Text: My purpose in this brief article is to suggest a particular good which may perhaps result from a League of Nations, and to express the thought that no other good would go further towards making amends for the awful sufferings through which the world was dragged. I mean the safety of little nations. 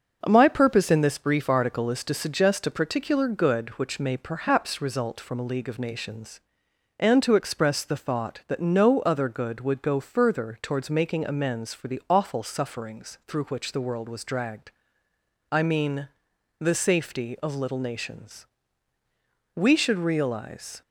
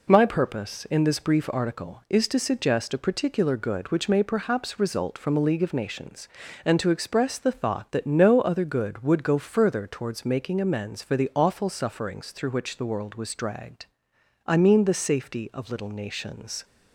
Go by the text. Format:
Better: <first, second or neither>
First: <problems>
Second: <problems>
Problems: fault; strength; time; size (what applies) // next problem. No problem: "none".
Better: second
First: starts louder than the rest; until 1.2 s; 6.5 dB // pauses between "mean" and "the"; noticeable; at 16.0 s; 0.52 s long // goes on to say "We should realize"; noticeable; from 19.5 s on; 1.2 s long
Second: none